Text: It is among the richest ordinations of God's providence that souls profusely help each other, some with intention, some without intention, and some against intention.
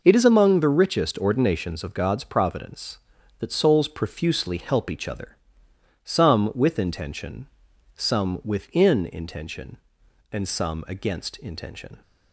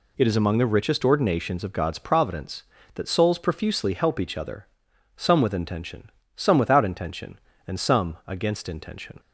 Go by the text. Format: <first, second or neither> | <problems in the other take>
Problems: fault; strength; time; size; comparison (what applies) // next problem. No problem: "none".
second | says "within" for "without"; at 8.4 s